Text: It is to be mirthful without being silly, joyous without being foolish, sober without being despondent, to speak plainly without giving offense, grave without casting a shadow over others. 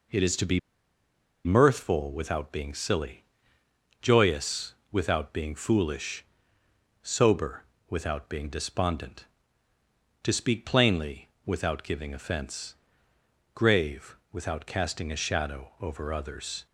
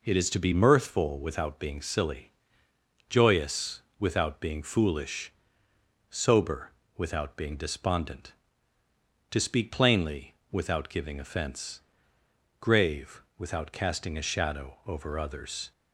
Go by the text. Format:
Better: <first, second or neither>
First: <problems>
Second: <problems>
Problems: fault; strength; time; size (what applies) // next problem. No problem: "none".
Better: second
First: pauses between "be" and "mirthful"; noticeable; at 0.5 s; 0.86 s long // pauses between "joyous" and "without"; slight; at 4.7 s; 0.16 s long // pauses between "sober" and "without"; slight; at 7.6 s; 0.26 s long // pauses between "plainly" and "without"; slight; at 11.2 s; 0.16 s long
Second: pauses between "joyous" and "without"; slight; at 3.8 s; 0.16 s long // pauses between "sober" and "without"; slight; at 6.7 s; 0.26 s long // pauses between "plainly" and "without"; slight; at 10.3 s; 0.16 s long